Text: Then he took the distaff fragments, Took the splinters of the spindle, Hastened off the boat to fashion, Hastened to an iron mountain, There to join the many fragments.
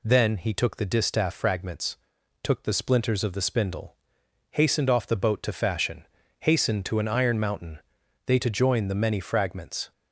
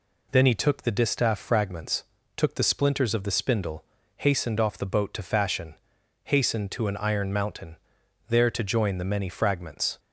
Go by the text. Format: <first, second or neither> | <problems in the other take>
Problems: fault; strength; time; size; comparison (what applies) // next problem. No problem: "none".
second | says "They" for "There"; at 8.2 s